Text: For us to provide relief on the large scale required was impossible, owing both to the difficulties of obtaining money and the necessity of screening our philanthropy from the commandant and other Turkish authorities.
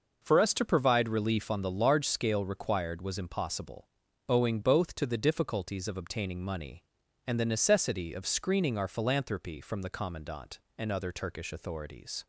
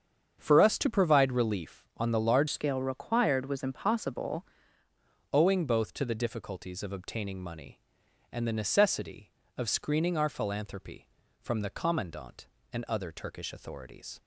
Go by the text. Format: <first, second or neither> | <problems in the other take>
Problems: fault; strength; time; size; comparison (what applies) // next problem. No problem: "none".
first | starts louder than the rest; strong; until 1.4 s; 7.5 dB // changes voice from "scale" to "impossible"; from 2.4 to 4.4 s; 2.0 s long